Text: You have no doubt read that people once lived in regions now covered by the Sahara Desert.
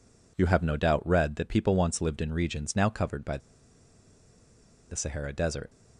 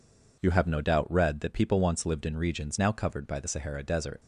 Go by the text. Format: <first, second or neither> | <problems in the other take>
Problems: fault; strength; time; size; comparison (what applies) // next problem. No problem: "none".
second | pauses between "by" and "the"; strong; at 3.3 s; 1.5 s long